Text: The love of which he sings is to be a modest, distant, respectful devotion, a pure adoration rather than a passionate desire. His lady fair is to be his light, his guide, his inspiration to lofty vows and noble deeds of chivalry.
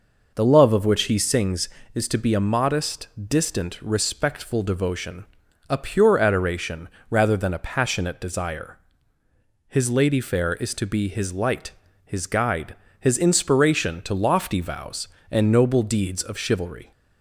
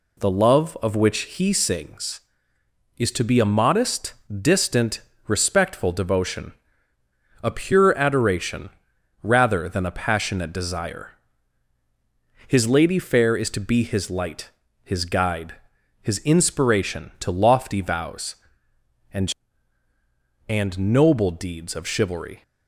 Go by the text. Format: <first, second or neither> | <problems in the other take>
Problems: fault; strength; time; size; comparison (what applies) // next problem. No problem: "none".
first | pauses between "adoration" and "rather"; noticeable; at 8.7 s; 0.52 s long; slight in the first // says "and" twice; at 20.4 s